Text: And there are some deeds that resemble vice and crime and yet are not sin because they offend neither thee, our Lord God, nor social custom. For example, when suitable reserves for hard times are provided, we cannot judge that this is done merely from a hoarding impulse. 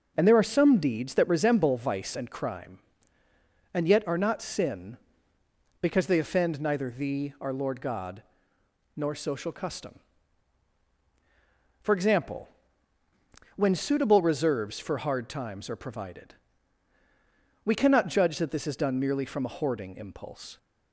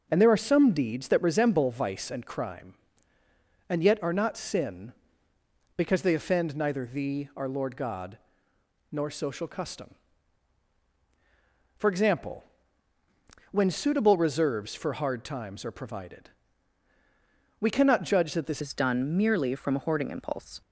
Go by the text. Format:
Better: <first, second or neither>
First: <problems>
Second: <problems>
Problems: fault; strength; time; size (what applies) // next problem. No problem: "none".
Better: first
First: none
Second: changes voice at "is"; from 18.6 s on; 2.0 s long